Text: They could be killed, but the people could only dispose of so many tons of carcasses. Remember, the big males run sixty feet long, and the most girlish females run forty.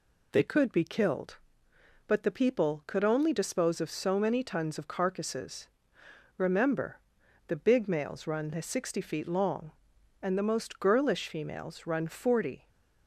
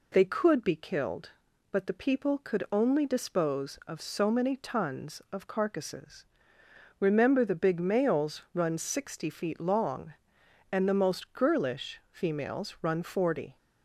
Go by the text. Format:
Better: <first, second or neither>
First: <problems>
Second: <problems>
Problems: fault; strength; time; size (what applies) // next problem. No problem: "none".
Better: neither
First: none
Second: none